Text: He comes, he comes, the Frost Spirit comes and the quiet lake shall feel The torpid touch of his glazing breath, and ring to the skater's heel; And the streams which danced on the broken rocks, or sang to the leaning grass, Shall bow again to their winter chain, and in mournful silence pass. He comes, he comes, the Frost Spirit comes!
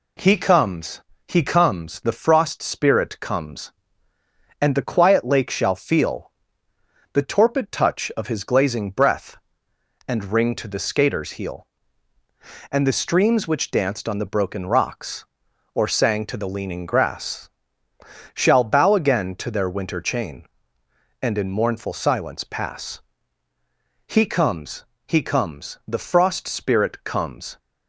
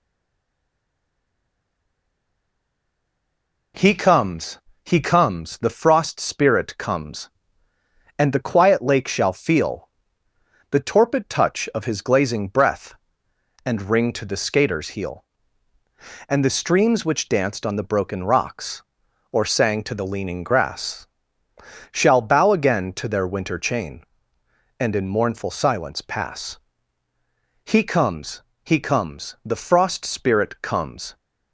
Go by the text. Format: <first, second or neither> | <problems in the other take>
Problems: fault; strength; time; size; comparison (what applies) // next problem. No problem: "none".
first | stays silent before the first word; strong; until 3.7 s; 3.7 s long // pauses between "feel" and "The"; noticeable; at 9.8 s; 0.80 s long; noticeable in the first